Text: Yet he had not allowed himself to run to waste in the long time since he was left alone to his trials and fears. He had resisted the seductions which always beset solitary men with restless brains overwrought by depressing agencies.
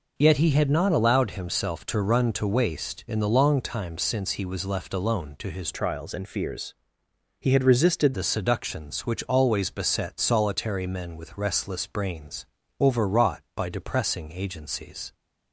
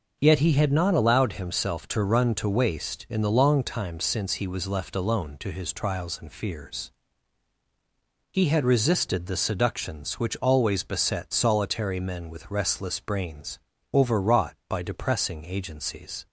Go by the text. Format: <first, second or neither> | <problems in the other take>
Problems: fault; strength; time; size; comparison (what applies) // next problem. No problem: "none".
second | changes voice from "trials" to "resisted"; from 5.7 to 8.1 s; 2.4 s long // pauses between "brains" and "overwrought"; slight; at 12.4 s; 0.36 s long; slight in the second